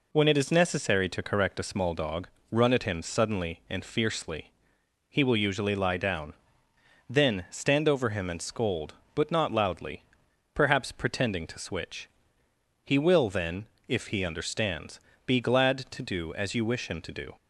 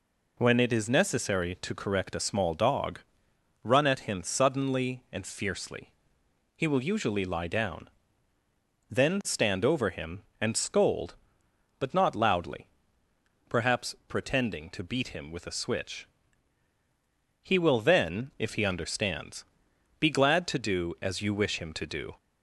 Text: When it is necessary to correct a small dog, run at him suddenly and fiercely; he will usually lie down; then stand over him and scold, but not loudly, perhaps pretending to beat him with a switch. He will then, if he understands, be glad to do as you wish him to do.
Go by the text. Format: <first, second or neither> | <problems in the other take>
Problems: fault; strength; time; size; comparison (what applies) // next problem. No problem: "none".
second | skips "beat him with a"; at 11.5 s